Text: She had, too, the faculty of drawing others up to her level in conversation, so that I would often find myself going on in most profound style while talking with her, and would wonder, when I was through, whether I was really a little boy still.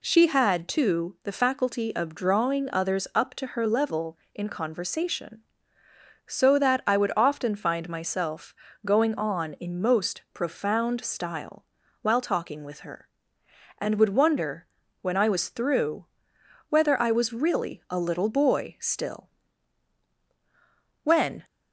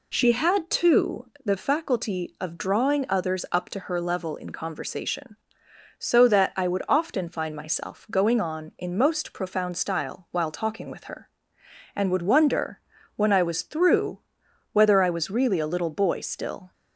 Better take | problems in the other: second | pauses between "myself" and "going"; slight; at 8.5 s; 0.32 s long // pauses between "style" and "while"; slight; at 11.6 s; 0.36 s long // goes on to say "When"; slight; from 21.0 s on; 0.40 s long

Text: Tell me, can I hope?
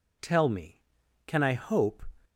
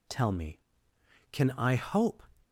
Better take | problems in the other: neither | none

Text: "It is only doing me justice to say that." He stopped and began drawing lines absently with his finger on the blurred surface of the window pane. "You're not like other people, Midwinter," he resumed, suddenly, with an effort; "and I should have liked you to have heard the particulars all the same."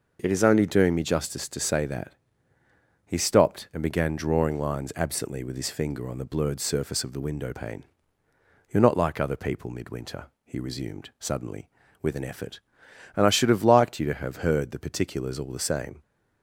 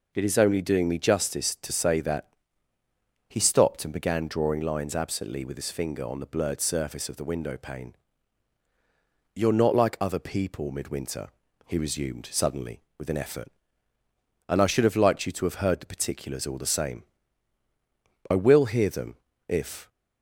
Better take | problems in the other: first | goes on to say "I will hear them if"; from 18.2 s on; 1.6 s long

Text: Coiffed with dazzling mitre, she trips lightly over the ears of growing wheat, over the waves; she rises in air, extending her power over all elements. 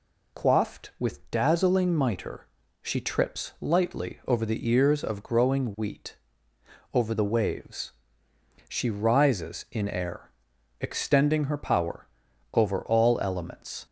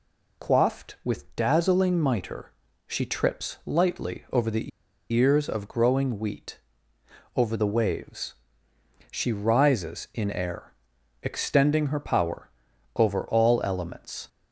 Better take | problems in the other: first | pauses between "the" and "ears"; at 4.7 s; 0.41 s long // pauses between "power" and "over"; noticeable; at 12.4 s; 0.46 s long; noticeable in the first

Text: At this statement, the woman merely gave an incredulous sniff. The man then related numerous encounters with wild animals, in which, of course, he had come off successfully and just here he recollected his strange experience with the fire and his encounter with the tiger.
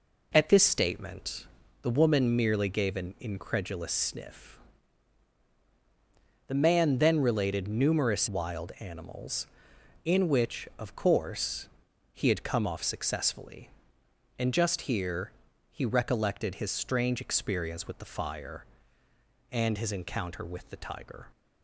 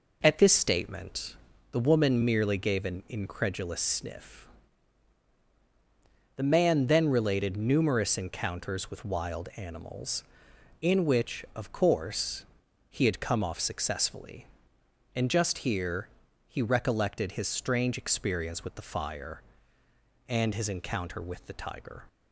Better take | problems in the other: second | skips "encounters with"; at 8.2 s // pauses between "here" and "he"; at 15.3 s; 0.40 s long; also in the second

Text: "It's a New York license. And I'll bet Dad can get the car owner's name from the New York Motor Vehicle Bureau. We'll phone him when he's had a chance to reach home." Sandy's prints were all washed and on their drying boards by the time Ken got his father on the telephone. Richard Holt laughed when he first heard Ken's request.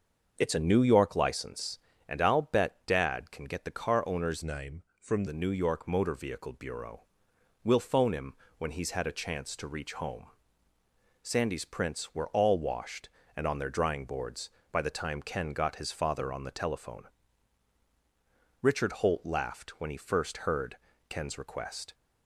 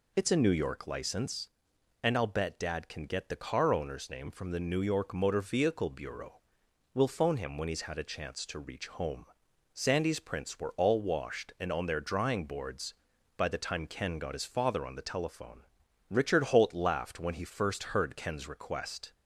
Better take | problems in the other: second | starts louder than the rest; until 1.3 s; 6.5 dB // changes voice from "name" to "from"; from 4.4 to 5.2 s; 0.8 s long // pauses between "him" and "when"; slight; at 8.3 s; 0.24 s long // pauses between "heard" and "Ken's"; slight; at 20.7 s; 0.32 s long

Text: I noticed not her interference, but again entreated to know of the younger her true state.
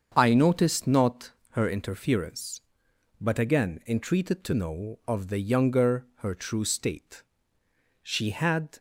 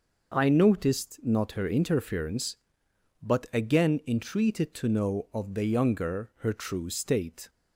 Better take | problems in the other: second | starts louder than the rest; until 1.1 s; 7 dB // pauses between "not" and "her"; slight; at 1.3 s; 0.20 s long // goes on to say "She had"; noticeable; from 8.0 s on; 0.76 s long

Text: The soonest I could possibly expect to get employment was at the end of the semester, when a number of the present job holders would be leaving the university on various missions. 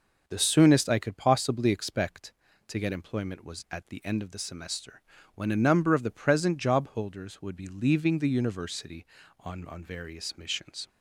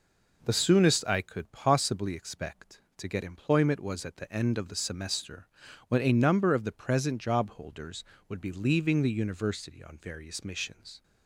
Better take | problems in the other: second | says "on" twice; at 9.6 s

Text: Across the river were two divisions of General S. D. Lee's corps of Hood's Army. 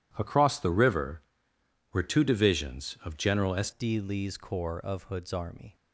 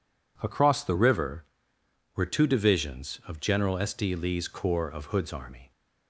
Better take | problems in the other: second | changes voice at "D"; from 3.7 s on; 2.0 s long

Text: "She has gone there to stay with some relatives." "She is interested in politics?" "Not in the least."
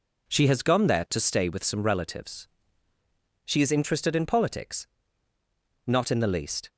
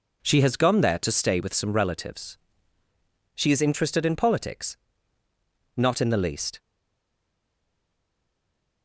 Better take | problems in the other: first | stays silent after the last word; from 6.5 s on; 2.3 s long

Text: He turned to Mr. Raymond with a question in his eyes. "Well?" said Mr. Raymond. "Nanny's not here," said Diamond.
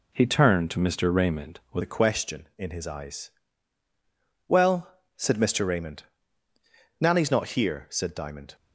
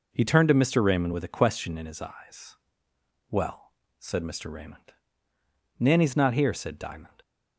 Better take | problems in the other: second | changes voice at "a"; from 1.8 s on; 6.7 s long

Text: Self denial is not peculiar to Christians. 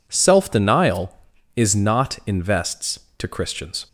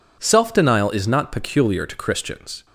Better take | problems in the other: second | says "invests" for "peculiar"; at 2.2 s

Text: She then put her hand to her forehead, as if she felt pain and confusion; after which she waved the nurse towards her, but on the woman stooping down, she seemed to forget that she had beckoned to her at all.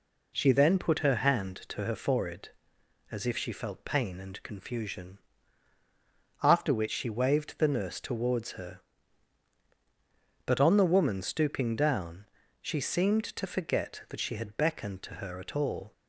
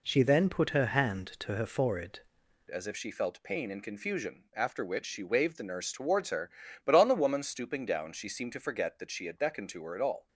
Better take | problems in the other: first | changes voice at "as"; from 2.6 s on; 7.6 s long

